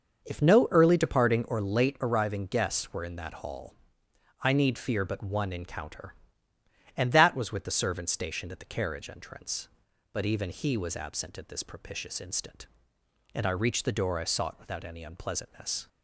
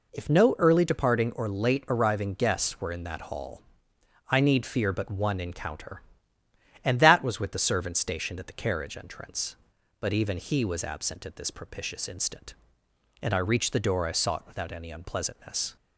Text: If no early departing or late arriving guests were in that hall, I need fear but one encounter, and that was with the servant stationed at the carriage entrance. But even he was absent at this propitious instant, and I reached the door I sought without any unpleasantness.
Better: second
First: starts louder than the rest; noticeable; until 2.0 s; 6 dB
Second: none

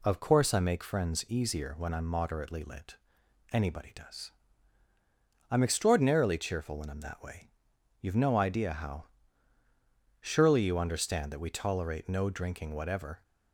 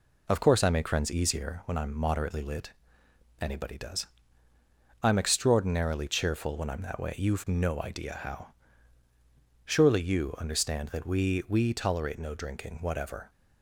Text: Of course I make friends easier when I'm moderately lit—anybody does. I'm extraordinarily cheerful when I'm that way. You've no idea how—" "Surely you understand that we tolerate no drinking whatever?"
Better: first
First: none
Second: says "we" twice; at 11.4 s

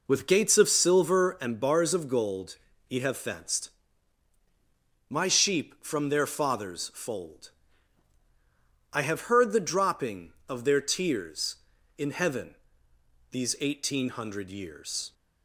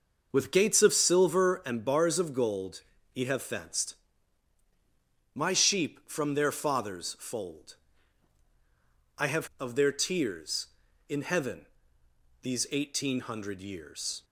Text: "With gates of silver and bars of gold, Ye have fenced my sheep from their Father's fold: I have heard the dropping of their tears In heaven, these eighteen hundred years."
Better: first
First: pauses between "fenced" and "my"; strong; at 3.7 s; 1.3 s long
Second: pauses between "fenced" and "my"; strong; at 3.9 s; 1.3 s long // skips "heard the dropping"; at 9.5 s

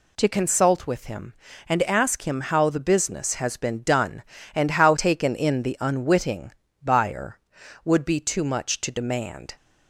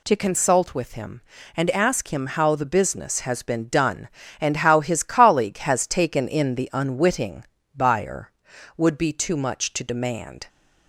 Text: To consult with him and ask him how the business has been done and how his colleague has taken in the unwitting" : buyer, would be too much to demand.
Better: second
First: skips "his colleague has"; at 4.9 s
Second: none

